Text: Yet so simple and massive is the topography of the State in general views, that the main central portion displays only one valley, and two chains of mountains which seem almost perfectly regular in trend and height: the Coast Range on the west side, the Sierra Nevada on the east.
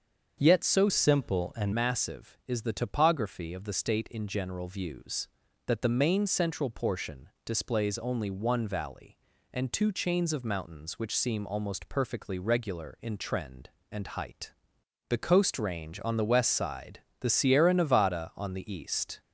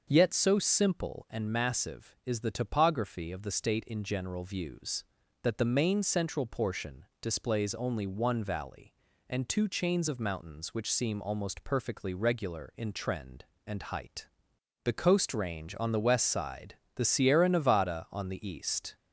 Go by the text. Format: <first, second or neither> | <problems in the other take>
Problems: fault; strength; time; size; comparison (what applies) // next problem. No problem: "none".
second | starts louder than the rest; until 1.4 s; 7 dB; also in the second // changes voice from "simple" to "and"; from 0.8 to 1.7 s; 0.9 s long // pauses between "portion" and "displays"; slight; at 7.2 s; 0.18 s long; slight in the second